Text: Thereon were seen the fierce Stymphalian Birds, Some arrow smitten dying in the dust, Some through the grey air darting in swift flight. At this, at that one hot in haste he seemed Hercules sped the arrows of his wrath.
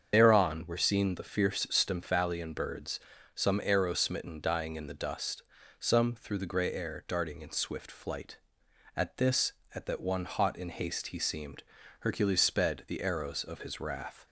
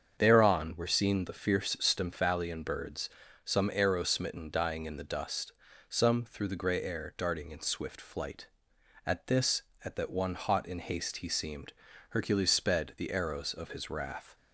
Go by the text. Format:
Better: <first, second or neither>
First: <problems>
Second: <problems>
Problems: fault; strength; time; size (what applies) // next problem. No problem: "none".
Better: second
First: loses the start of "Thereon"; at 0.1 s; 40 ms // starts louder than the rest; strong; until 1.1 s; 7 dB // pauses between "seemed" and "Hercules"; slight; at 11.6 s; 0.36 s long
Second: starts louder than the rest; strong; until 1.2 s; 7 dB // pauses between "seemed" and "Hercules"; slight; at 11.7 s; 0.36 s long